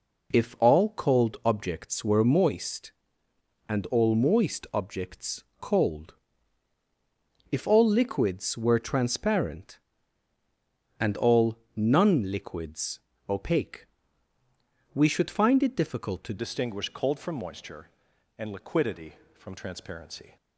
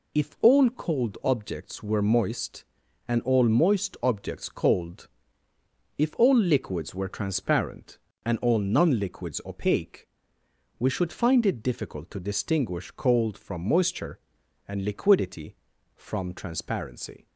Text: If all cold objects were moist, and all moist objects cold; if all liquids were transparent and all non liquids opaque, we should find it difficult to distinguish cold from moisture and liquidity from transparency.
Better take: second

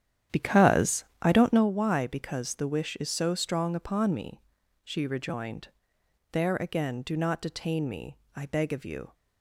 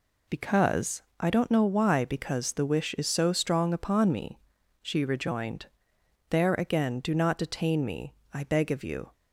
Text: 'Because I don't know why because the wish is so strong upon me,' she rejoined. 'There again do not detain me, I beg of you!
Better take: second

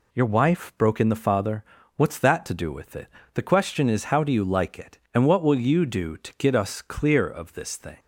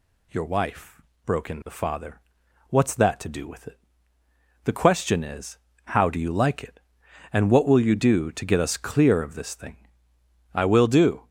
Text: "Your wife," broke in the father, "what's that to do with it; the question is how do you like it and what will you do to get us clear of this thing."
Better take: first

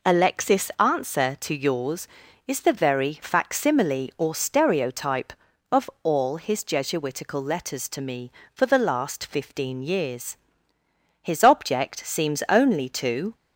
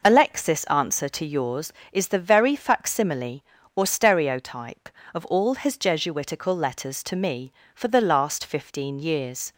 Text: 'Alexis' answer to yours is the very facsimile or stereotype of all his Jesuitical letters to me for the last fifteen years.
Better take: second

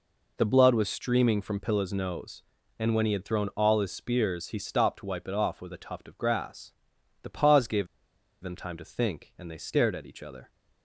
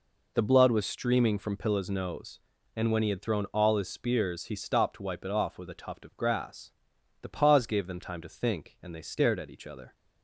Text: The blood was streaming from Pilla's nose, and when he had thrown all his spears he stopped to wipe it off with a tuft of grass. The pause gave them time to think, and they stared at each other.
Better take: second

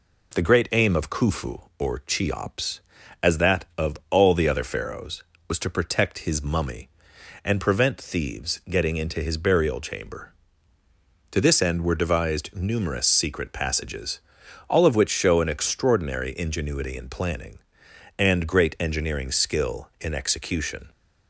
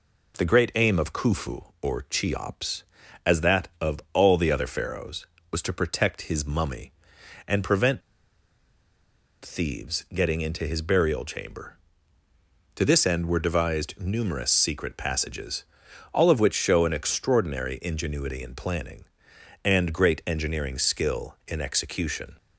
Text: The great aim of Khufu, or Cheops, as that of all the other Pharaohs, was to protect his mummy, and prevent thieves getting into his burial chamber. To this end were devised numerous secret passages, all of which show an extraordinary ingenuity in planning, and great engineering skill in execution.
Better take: first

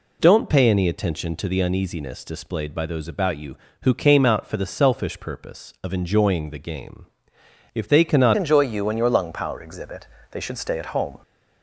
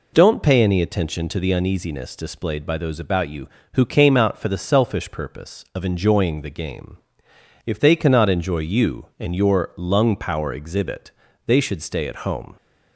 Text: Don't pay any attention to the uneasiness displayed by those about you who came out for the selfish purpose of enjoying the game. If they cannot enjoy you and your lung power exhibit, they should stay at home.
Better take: second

